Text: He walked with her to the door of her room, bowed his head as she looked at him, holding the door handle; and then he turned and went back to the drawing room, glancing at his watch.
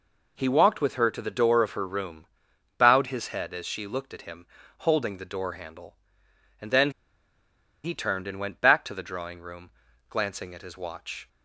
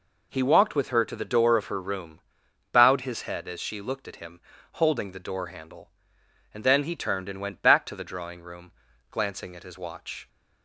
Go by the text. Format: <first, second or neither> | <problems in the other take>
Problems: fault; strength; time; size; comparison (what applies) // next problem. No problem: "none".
second | pauses between "then" and "he"; noticeable; at 6.9 s; 0.93 s long